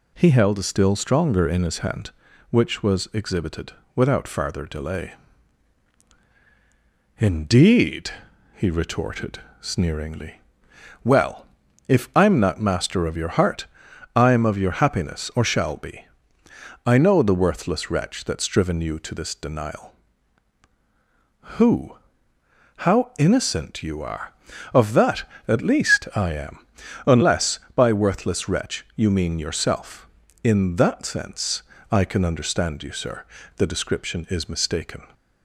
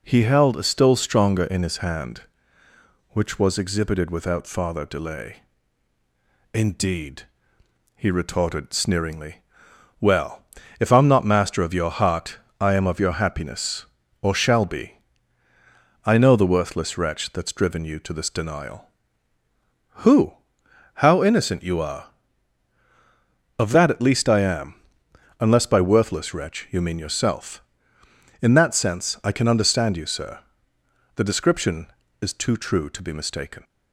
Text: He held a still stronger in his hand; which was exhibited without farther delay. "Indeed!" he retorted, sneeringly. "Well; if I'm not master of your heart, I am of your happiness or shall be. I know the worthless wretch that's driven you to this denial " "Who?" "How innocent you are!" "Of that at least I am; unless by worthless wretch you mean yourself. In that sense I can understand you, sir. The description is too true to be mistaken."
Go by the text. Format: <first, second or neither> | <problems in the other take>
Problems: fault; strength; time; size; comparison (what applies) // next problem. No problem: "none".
second | pauses between "exhibited" and "without"; slight; at 3.7 s; 0.24 s long // pauses between "sense" and "I"; slight; at 31.6 s; 0.28 s long // skips "too true to be"; at 34.4 s